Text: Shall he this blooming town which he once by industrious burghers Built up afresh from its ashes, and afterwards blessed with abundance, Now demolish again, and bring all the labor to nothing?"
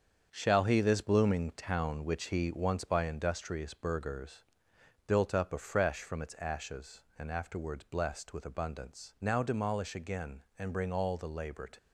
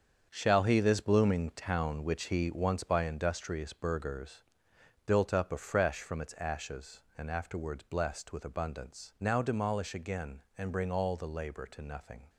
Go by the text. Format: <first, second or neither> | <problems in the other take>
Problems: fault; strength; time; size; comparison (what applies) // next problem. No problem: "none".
second | starts louder than the rest; strong; until 1.3 s; 7.5 dB; strong in the second // pauses between "burghers" and "Built"; noticeable; at 4.4 s; 0.64 s long; noticeable in the second // stops before "nothing"; at 11.7 s